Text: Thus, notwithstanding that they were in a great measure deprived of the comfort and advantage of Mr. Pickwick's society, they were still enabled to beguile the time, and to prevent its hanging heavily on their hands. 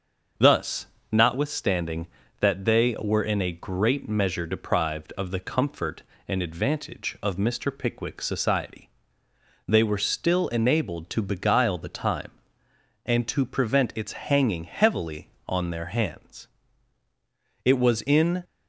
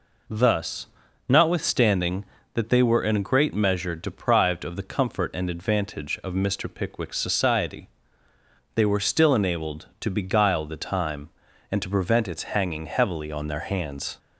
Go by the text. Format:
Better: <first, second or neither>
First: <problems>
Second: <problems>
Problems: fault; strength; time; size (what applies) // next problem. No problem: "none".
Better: second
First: starts louder than the rest; until 1.6 s; 6.5 dB // goes on to say "It was in"; noticeable; from 17.6 s on; 0.80 s long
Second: none